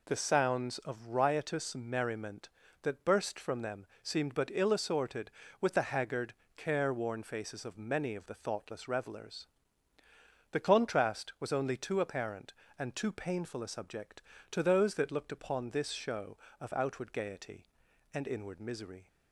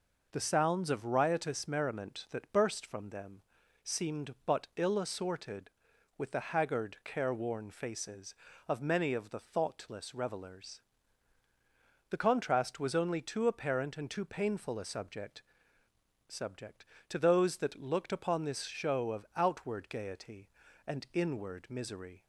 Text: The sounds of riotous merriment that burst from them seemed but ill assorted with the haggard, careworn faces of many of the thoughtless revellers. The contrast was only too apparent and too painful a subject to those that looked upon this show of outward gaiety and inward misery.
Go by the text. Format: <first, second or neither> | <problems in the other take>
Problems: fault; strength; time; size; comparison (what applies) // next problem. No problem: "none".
first | pauses between "them" and "seemed"; at 3.4 s; 0.42 s long; slight in the first // says "subject" twice; at 16.3 s